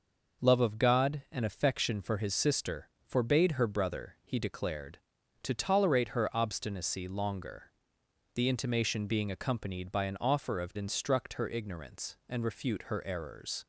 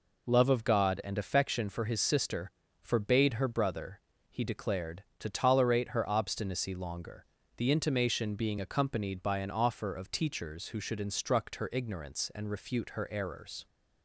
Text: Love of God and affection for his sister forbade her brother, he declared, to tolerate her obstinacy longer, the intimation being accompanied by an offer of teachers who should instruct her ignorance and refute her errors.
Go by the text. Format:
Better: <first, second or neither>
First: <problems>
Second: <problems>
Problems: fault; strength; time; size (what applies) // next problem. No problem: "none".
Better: second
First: pauses between "sister" and "forbade"; slight; at 2.8 s; 0.18 s long // skips "teachers who should"; at 10.7 s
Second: pauses between "sister" and "forbade"; slight; at 2.5 s; 0.28 s long